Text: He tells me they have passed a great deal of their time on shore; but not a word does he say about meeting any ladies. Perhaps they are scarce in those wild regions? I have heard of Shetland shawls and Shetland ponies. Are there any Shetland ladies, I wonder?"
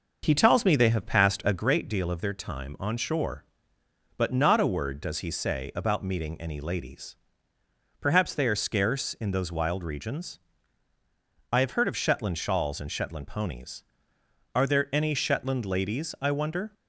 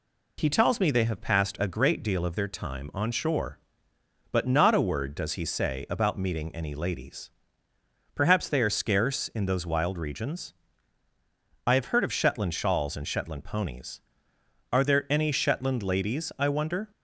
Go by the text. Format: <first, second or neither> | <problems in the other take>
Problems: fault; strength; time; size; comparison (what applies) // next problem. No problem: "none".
second | starts louder than the rest; noticeable; until 1.7 s; 6 dB